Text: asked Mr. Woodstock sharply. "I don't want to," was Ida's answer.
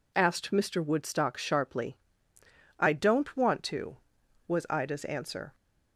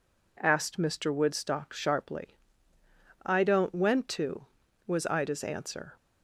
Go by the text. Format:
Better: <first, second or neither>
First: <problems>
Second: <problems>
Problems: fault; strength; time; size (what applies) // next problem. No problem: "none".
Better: first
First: none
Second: says "went" for "want"; at 3.7 s